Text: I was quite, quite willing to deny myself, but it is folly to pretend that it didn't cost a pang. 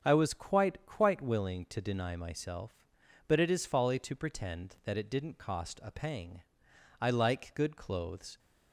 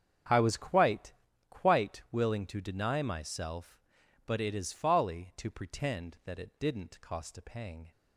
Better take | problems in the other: second | starts louder than the rest; until 1.0 s; 6.5 dB; strong in the second // goes on to say "I like good clothes"; from 6.9 s on; 1.4 s long

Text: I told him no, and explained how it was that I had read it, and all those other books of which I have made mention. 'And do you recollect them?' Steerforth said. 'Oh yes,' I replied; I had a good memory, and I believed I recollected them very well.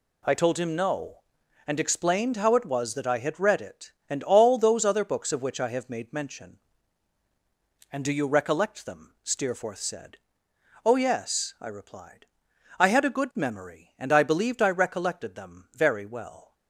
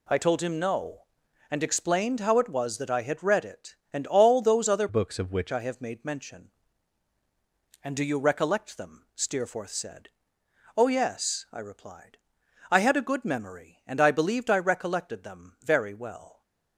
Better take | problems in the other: first | changes voice from "books" to "which"; from 4.8 to 5.5 s; 0.7 s long

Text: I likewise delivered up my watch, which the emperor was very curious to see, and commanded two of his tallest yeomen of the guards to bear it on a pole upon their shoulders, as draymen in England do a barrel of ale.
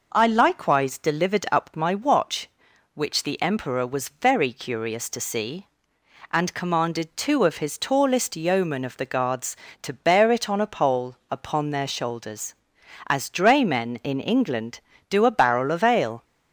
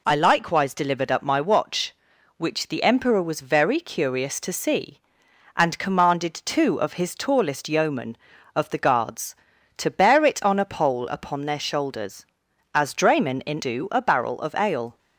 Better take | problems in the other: first | skips "England"; at 13.6 s

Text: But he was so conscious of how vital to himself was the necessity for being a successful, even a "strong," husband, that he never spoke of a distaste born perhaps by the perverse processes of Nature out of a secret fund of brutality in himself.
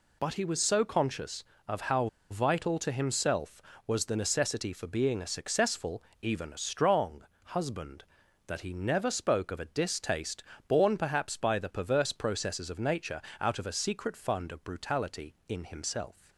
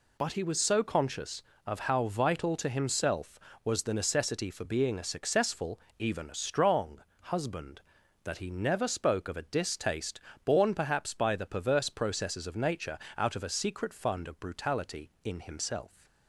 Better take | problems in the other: second | pauses between "how" and "vital"; slight; at 2.0 s; 0.23 s long // pauses between "distaste" and "born"; slight; at 10.4 s; 0.24 s long; slight in the second // pauses between "Nature" and "out"; slight; at 13.2 s; 0.18 s long; slight in the second

